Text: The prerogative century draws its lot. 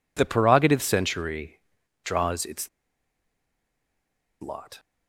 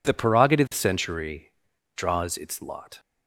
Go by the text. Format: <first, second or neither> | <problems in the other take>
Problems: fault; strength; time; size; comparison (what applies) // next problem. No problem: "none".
second | pauses between "century" and "draws"; at 1.5 s; 0.44 s long; also in the second // pauses between "its" and "lot"; strong; at 2.6 s; 1.7 s long